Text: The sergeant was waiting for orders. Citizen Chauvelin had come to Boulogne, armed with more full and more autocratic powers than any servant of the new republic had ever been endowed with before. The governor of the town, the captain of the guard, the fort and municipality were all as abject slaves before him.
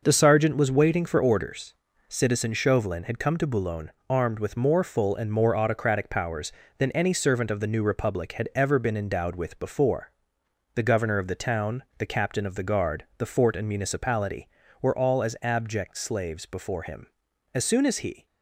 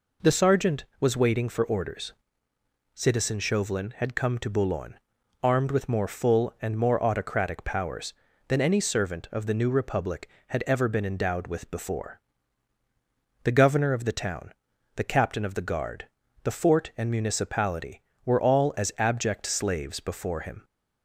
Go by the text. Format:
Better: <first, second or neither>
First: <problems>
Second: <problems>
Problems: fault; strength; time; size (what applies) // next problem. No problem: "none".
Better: second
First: goes on to say "As soon as he"; noticeable; from 17.5 s on; 0.72 s long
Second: none